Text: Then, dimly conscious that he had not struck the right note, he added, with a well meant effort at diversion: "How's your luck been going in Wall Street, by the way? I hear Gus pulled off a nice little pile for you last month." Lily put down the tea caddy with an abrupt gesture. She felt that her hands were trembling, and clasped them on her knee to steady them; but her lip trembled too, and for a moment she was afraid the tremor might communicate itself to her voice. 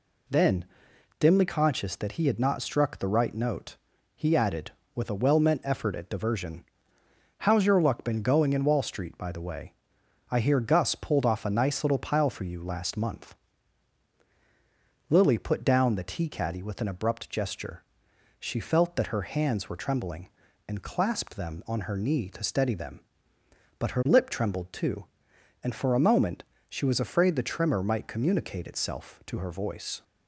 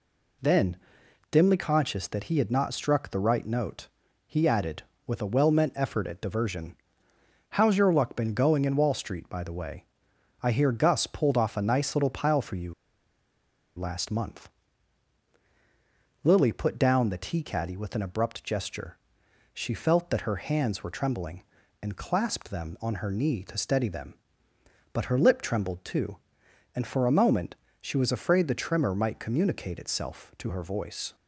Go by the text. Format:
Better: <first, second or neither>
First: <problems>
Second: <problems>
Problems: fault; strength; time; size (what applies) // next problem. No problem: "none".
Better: first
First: pauses between "moment" and "she"; slight; at 26.4 s; 0.26 s long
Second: pauses between "you" and "last"; at 12.7 s; 1.0 s long // pauses between "moment" and "she"; slight; at 27.5 s; 0.26 s long